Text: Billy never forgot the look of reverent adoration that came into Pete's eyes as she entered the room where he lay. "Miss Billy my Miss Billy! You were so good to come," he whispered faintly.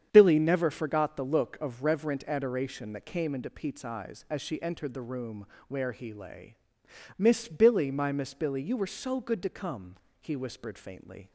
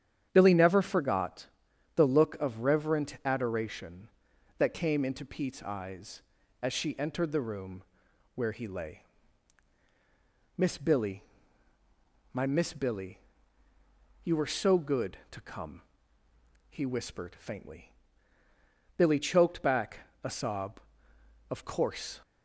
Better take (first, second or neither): first